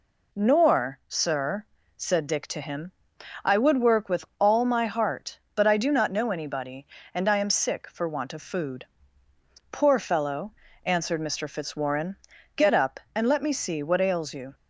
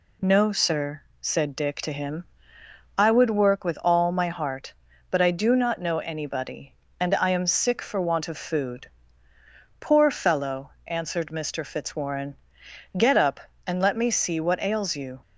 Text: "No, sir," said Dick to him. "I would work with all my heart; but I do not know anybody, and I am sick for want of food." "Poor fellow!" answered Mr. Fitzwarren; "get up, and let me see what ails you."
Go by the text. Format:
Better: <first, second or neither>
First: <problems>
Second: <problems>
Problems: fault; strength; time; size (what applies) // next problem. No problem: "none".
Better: second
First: says "Nor" for "No"; at 0.3 s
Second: none